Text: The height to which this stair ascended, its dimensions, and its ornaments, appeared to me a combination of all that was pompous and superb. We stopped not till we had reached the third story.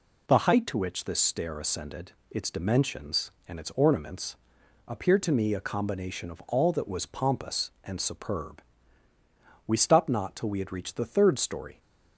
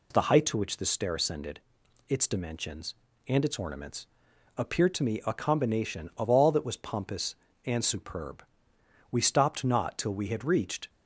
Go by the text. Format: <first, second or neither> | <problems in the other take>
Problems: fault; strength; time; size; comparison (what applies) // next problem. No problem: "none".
first | stops before "the third story"; at 10.8 s